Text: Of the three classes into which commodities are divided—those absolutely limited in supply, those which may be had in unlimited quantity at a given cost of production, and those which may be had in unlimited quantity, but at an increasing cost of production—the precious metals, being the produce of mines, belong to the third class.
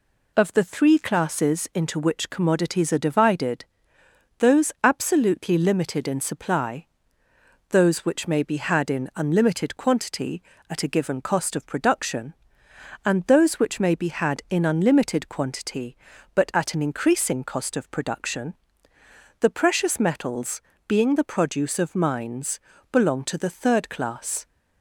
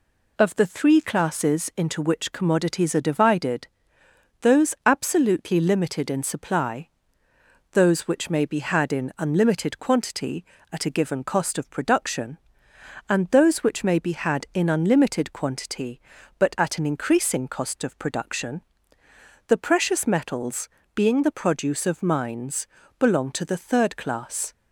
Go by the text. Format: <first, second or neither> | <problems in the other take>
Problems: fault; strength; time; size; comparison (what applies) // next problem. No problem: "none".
neither | none